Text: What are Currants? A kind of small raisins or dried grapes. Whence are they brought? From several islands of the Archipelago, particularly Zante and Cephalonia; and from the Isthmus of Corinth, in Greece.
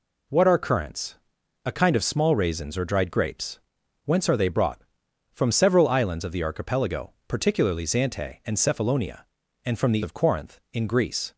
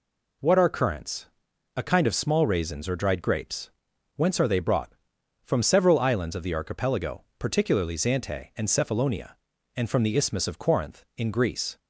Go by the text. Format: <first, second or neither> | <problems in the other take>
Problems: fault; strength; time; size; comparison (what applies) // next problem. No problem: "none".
second | skips "Isthmus"; at 10.0 s